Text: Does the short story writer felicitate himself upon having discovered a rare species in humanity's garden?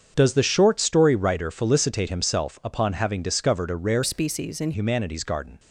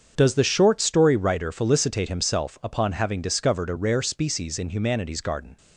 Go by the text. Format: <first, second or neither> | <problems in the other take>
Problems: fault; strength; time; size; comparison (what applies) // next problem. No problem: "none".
second | starts louder than the rest; strong; until 1.1 s; 7 dB; also in the second // changes voice from "species" to "in"; from 4.0 to 4.7 s; 0.7 s long